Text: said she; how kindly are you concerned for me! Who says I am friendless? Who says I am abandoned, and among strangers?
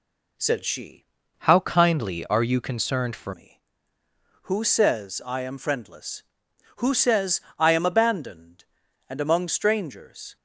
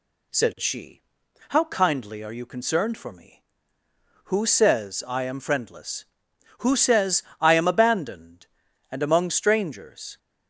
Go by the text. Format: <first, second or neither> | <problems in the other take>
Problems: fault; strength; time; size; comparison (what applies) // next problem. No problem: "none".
second | changes voice from "how" to "for"; from 1.3 to 3.3 s; 2.0 s long // pauses between "says" and "I"; slight; at 7.3 s; 0.18 s long; slight in the second